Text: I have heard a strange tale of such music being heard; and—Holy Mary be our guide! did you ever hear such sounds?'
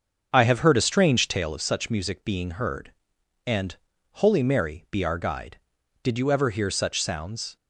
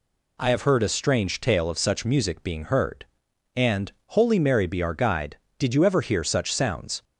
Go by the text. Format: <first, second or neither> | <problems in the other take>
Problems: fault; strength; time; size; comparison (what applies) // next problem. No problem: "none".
second | starts louder than the rest; until 1.5 s; 6.5 dB